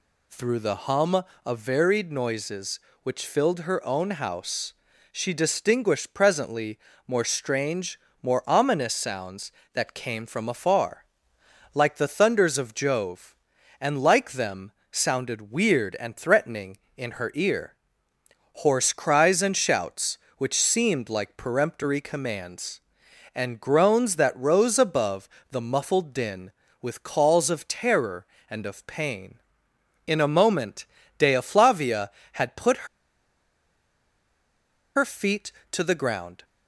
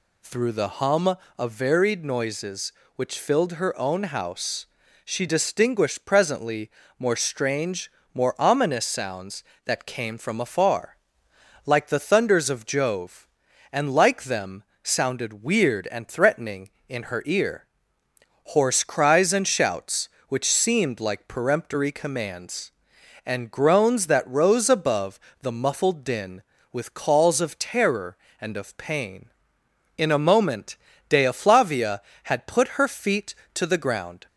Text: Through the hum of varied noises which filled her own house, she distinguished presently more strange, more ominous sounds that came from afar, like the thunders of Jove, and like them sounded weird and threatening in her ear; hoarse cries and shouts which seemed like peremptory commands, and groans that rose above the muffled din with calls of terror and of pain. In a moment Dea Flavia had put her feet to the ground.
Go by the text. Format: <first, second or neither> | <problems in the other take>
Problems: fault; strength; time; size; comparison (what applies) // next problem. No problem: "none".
second | pauses between "presently" and "more"; slight; at 6.7 s; 0.30 s long; slight in the second // pauses between "them" and "sounded"; slight; at 14.7 s; 0.20 s long; slight in the second // pauses between "above" and "the"; slight; at 25.2 s; 0.22 s long; slight in the second // pauses between "moment" and "Dea"; slight; at 30.8 s; 0.32 s long; slight in the second // pauses between "put" and "her"; strong; at 32.8 s; 2.0 s long